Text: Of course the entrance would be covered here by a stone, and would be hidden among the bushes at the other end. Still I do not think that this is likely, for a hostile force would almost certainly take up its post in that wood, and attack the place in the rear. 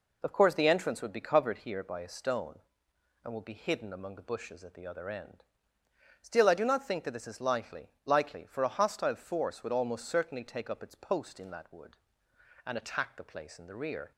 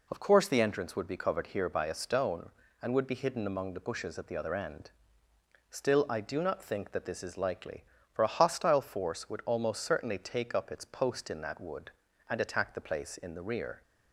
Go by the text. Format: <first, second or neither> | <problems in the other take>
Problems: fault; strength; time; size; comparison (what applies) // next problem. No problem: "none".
second | says "likely" twice; at 8.0 s